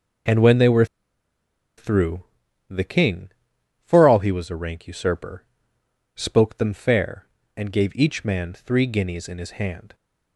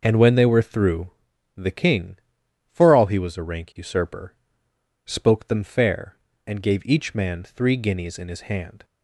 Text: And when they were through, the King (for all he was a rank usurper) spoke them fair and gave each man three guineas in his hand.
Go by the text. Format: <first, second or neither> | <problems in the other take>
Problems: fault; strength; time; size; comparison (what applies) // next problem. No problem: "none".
second | pauses between "were" and "through"; noticeable; at 0.8 s; 0.92 s long